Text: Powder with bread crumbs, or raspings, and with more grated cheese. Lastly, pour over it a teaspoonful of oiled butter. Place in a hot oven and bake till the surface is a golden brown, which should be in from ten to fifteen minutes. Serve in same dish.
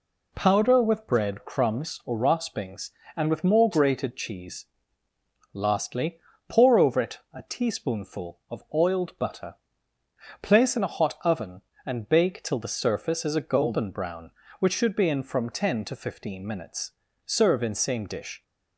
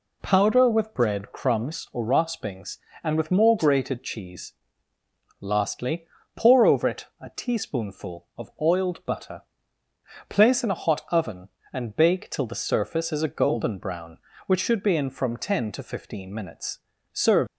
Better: first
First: none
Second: stops before "in same dish"; at 17.4 s

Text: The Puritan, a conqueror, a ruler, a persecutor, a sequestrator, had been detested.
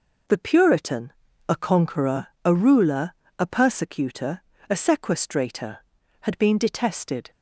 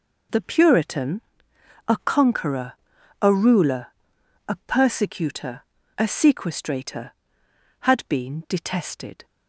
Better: neither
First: none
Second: none

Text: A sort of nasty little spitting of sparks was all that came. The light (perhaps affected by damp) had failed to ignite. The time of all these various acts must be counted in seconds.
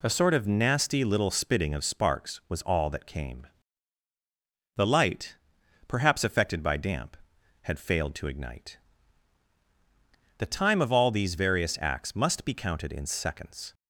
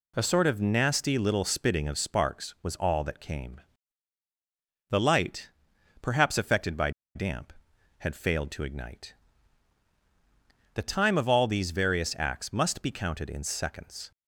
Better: first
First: none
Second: pauses between "by" and "damp"; slight; at 6.9 s; 0.24 s long

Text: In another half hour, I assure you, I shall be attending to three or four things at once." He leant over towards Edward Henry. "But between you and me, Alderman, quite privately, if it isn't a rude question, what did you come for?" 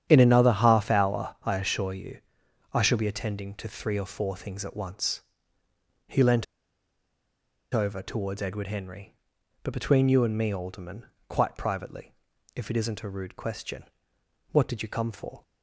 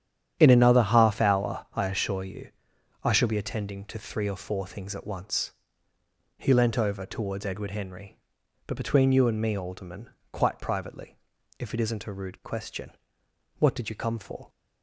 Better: second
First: starts louder than the rest; strong; until 1.1 s; 9.5 dB // pauses between "leant" and "over"; strong; at 6.4 s; 1.2 s long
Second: starts louder than the rest; strong; until 1.4 s; 9.5 dB

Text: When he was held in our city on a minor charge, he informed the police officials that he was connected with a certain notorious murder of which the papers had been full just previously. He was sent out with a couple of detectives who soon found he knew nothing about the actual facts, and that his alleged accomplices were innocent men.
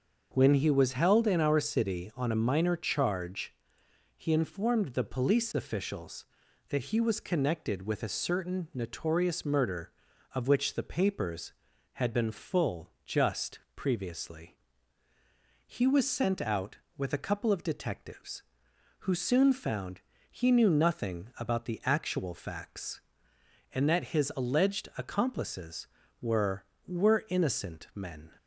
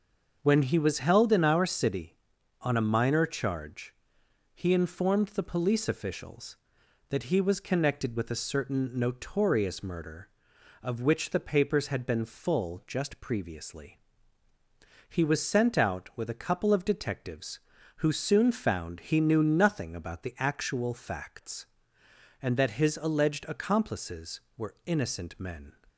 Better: second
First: starts louder than the rest; until 1.3 s; 6.5 dB // pauses between "just" and "previously"; slight; at 13.5 s; 0.16 s long // pauses between "found" and "he"; slight; at 19.9 s; 0.32 s long // says "were" twice; at 26.8 s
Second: starts louder than the rest; until 1.4 s; 6.5 dB

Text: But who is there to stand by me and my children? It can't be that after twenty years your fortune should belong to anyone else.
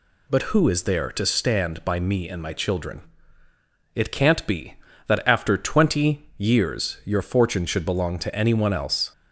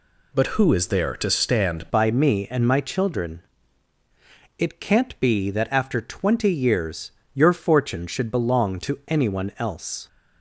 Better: first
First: none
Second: changes voice at "by"; from 1.9 s on; 8.1 s long // pauses between "years" and "your"; slight; at 7.1 s; 0.22 s long

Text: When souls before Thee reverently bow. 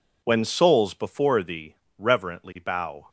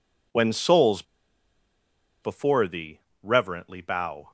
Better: first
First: pauses between "Thee" and "reverently"; slight; at 1.7 s; 0.24 s long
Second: pauses between "souls" and "before"; at 1.0 s; 1.1 s long // pauses between "Thee" and "reverently"; slight; at 2.9 s; 0.24 s long

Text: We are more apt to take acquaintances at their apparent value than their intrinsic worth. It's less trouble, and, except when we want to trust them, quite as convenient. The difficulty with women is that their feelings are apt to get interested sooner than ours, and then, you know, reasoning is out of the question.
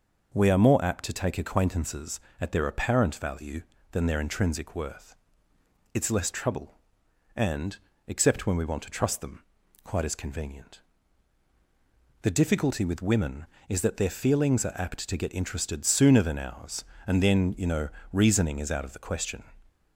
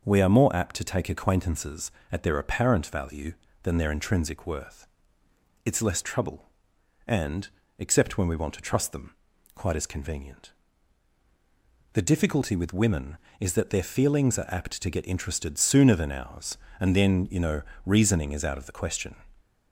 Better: neither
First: none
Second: none

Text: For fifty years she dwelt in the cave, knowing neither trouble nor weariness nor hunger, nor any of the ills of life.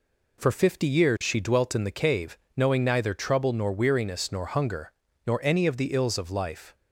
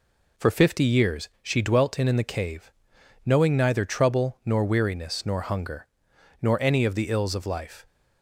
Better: first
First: none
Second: says "in" twice; at 2.0 s

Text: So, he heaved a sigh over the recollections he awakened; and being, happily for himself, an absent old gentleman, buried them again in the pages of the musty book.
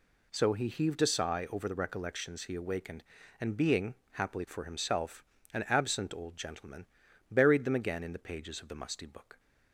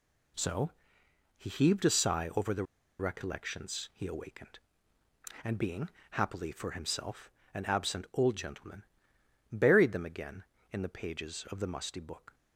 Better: first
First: none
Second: pauses between "the" and "recollections"; slight; at 2.6 s; 0.34 s long

